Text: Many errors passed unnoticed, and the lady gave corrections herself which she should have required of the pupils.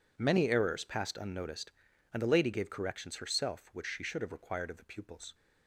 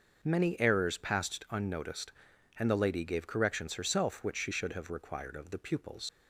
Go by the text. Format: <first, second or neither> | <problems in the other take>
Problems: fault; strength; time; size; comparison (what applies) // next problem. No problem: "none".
first | starts louder than the rest; noticeable; until 1.2 s; 6 dB // leaves "pupils" unfinished; at 6.0 s; 85 ms